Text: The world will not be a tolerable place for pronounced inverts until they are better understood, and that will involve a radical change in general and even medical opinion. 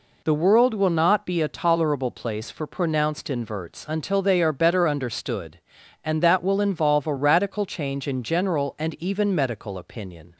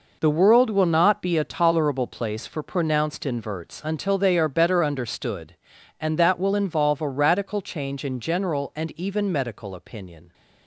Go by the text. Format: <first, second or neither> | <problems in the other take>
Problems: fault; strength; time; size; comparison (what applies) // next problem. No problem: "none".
first | gets quieter; strong; throughout; 10 dB